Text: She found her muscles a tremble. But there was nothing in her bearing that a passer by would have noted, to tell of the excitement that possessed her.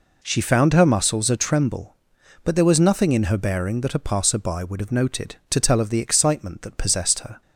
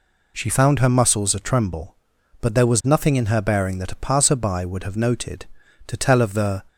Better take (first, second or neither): first